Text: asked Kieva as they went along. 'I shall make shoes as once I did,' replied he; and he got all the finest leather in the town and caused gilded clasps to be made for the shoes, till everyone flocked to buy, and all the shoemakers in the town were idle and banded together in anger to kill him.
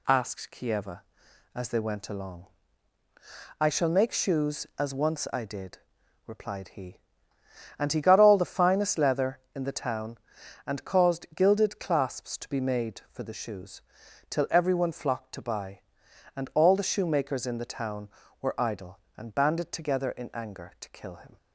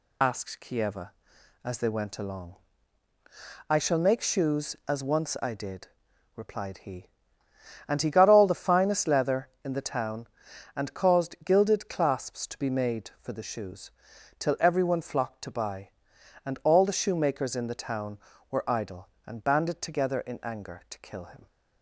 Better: first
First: none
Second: loses the start of "asked"; at 0.2 s; 45 ms

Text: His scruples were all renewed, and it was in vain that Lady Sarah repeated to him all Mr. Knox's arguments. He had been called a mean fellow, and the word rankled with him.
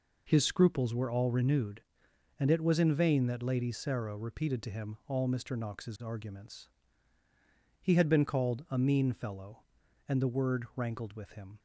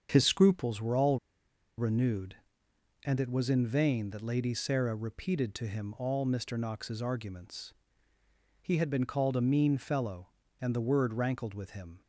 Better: first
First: none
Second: starts louder than the rest; strong; until 1.1 s; 7 dB // pauses between "all" and "renewed"; noticeable; at 1.1 s; 0.60 s long

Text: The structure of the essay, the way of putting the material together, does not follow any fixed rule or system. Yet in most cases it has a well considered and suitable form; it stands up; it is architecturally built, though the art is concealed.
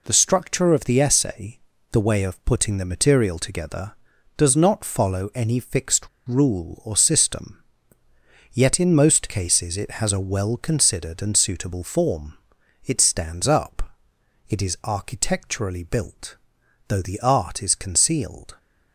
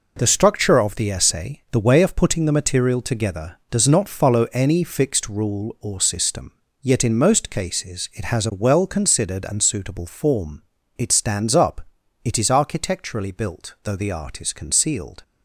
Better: second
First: pauses between "fixed" and "rule"; slight; at 6.0 s; 0.19 s long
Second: none

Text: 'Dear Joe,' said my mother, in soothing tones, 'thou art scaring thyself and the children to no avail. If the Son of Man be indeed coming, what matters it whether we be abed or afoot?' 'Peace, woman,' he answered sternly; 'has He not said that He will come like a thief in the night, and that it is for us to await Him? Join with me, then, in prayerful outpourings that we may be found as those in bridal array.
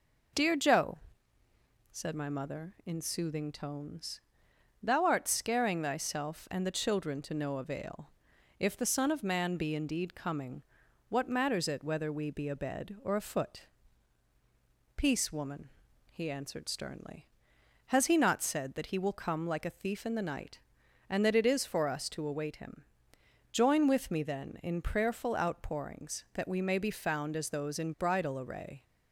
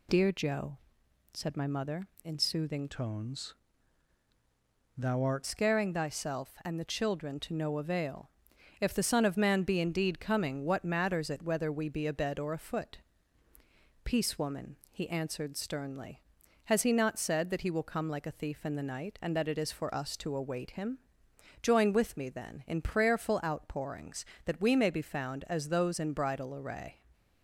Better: first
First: none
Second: changes voice from "tones" to "art"; from 2.8 to 5.4 s; 2.6 s long

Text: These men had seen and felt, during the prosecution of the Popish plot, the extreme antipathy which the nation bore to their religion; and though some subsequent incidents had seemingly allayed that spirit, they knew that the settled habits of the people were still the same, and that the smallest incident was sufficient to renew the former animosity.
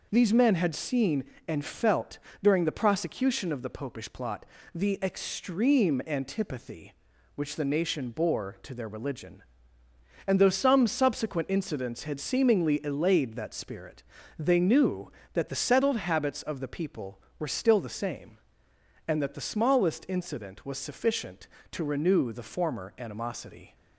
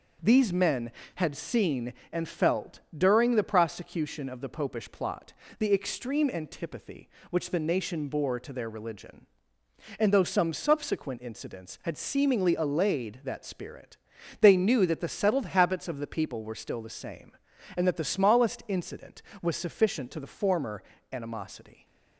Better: first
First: none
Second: skips "renew"; at 20.1 s // pauses between "former" and "animosity"; slight; at 20.8 s; 0.30 s long

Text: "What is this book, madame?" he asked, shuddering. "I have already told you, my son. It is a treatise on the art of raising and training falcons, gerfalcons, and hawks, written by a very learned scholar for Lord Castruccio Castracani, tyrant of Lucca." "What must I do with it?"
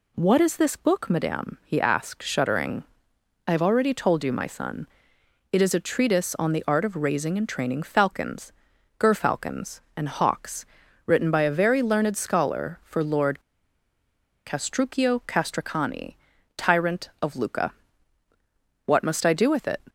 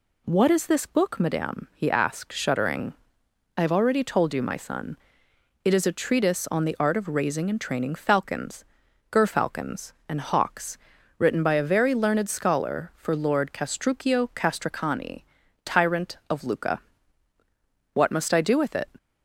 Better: second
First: pauses between "Lord" and "Castruccio"; at 13.3 s; 1.0 s long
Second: none

